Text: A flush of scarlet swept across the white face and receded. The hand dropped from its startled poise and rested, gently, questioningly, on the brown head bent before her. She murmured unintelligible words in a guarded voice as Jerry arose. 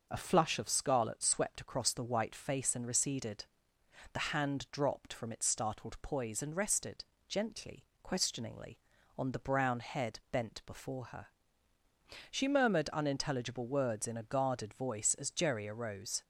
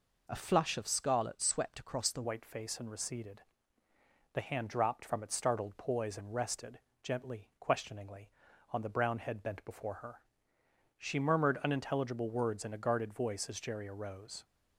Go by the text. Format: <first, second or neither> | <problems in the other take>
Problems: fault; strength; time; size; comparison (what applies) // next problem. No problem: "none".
first | changes voice at "white"; from 2.2 s on; 12.2 s long